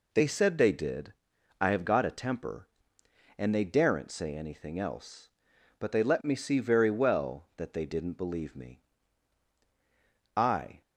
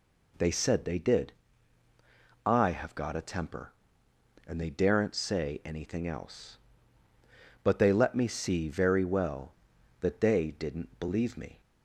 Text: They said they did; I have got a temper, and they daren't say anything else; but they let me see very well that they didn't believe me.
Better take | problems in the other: second | goes on to say "I"; slight; from 10.3 s on; 0.44 s long

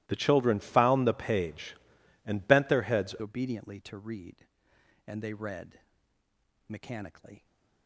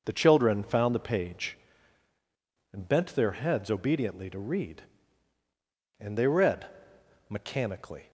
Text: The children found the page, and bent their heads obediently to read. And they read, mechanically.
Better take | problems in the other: second | starts louder than the rest; strong; until 1.0 s; 17.5 dB // changes voice at "obediently"; from 3.1 s on; 4.3 s long

